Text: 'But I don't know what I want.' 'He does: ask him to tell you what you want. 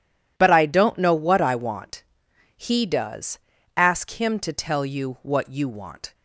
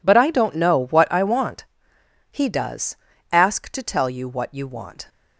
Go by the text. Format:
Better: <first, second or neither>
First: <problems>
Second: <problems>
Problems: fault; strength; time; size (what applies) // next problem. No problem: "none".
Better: first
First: none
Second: skips "him"; at 3.6 s